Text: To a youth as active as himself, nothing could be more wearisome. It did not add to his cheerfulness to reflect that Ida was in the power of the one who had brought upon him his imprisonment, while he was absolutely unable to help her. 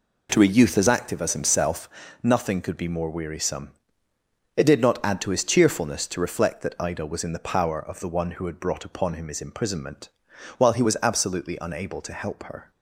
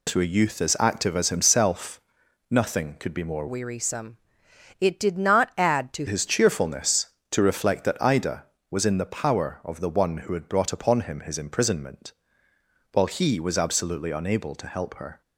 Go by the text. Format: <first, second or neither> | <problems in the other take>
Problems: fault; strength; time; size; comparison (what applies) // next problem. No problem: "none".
first | changes voice from "wearisome" to "to"; from 3.4 to 6.0 s; 2.6 s long